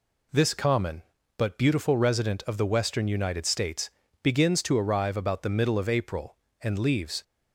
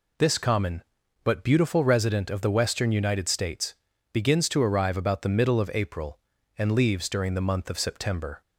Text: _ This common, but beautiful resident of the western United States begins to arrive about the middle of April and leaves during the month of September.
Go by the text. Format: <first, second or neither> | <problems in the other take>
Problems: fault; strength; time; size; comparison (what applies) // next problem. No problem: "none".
second | pauses between "States" and "begins"; slight; at 3.8 s; 0.32 s long; also in the second // stops before "during the month of September"; at 7.2 s